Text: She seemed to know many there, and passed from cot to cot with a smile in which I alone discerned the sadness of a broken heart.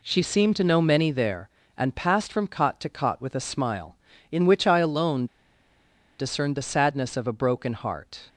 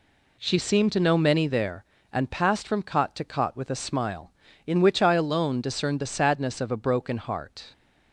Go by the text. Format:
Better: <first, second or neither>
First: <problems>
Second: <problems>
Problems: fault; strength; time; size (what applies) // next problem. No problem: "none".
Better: second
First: pauses between "alone" and "discerned"; noticeable; at 5.2 s; 0.93 s long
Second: none